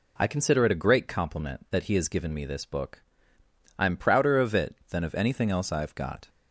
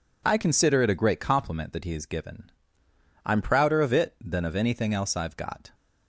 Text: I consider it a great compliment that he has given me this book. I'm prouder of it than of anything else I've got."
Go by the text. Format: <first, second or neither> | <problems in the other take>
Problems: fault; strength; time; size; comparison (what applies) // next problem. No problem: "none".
first | skips "me this book"; at 2.8 s